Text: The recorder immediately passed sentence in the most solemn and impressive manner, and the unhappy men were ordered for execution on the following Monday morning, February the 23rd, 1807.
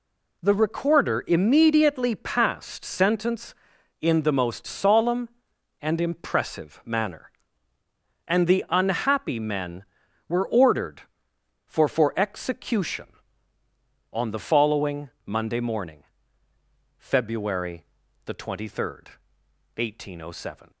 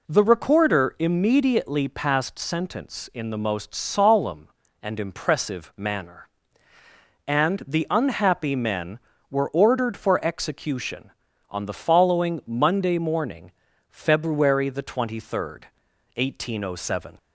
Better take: second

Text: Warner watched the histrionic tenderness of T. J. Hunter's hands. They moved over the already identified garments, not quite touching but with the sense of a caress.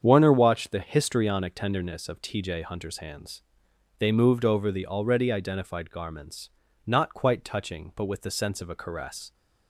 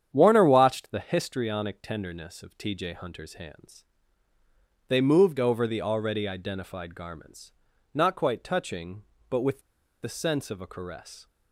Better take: first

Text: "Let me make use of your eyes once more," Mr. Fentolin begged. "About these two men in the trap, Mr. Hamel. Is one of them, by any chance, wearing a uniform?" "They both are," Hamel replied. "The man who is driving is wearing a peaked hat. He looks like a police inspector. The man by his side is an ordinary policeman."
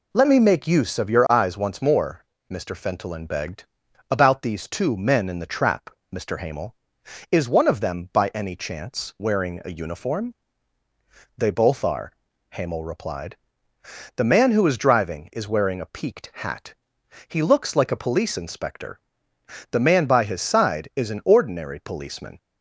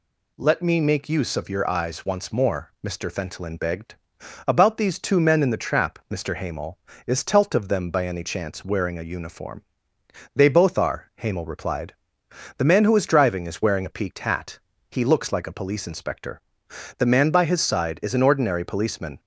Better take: first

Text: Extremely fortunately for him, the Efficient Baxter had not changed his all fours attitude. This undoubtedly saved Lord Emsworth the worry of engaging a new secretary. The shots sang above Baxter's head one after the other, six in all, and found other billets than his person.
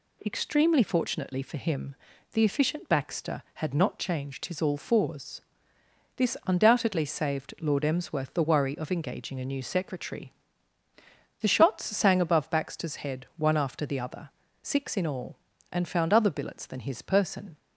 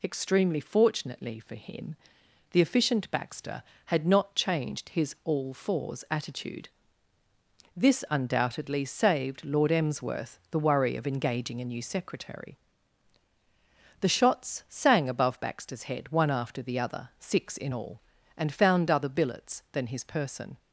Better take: second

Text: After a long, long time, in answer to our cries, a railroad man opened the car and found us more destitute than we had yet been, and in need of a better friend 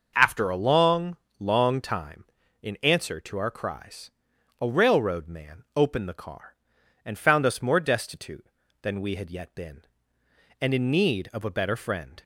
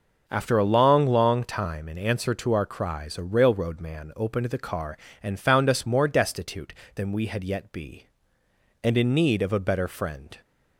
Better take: first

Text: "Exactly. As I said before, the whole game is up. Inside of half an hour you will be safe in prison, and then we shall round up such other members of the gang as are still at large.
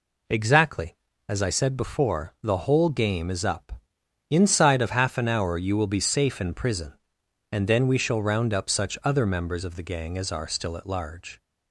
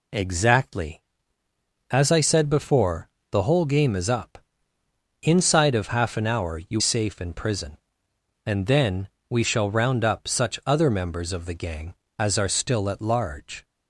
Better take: first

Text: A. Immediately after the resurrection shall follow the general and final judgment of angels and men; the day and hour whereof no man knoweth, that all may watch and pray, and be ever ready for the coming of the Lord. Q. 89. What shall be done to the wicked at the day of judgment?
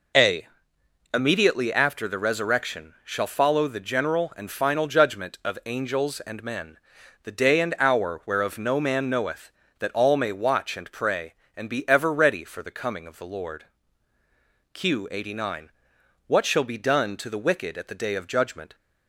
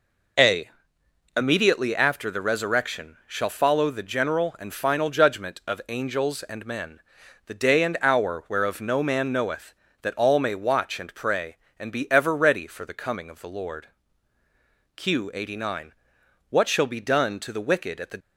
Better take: first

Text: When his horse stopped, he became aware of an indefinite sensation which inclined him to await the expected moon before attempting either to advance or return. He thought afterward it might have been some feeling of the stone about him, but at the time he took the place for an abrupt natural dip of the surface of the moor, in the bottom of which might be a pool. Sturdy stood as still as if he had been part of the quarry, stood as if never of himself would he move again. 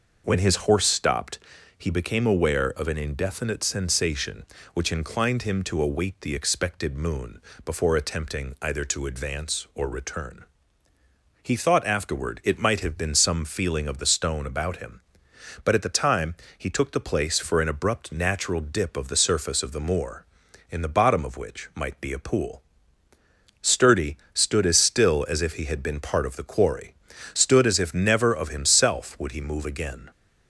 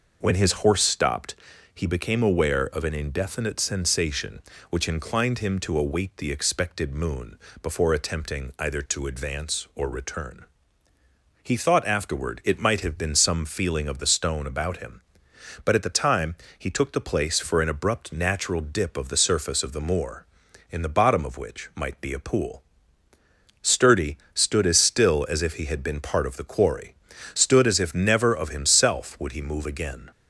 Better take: neither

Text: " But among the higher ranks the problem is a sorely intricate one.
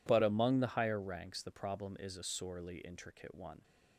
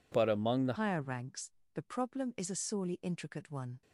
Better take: first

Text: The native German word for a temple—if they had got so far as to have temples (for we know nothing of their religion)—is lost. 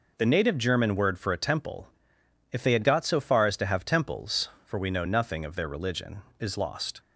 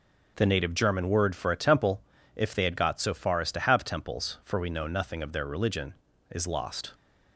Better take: neither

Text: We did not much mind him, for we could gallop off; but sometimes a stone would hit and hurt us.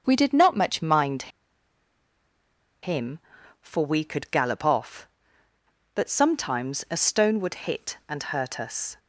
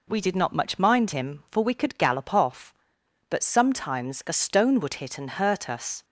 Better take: second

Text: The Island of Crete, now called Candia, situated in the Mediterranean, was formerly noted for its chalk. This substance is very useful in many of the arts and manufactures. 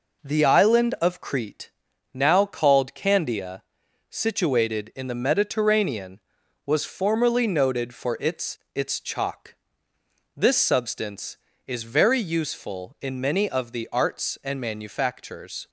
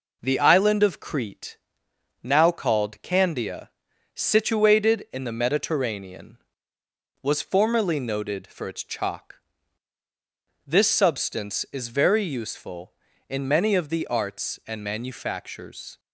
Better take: second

